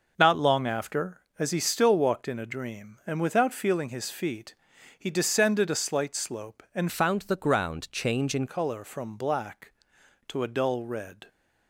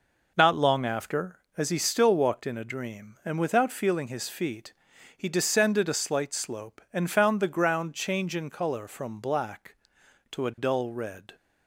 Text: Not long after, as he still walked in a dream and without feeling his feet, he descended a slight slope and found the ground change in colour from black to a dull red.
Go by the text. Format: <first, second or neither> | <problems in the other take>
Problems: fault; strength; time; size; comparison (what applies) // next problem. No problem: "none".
second | changes voice from "found" to "in"; from 6.8 to 8.4 s; 1.6 s long